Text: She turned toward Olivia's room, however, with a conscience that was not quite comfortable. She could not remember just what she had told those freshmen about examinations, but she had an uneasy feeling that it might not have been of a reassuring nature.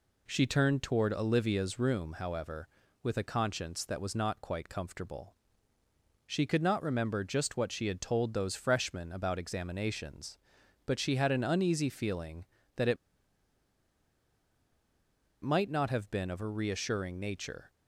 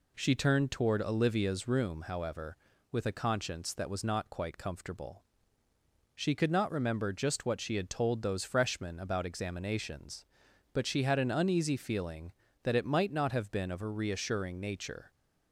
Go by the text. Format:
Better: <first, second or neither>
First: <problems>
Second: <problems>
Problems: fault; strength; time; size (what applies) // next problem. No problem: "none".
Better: second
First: pauses between "it" and "might"; strong; at 12.9 s; 2.4 s long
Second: none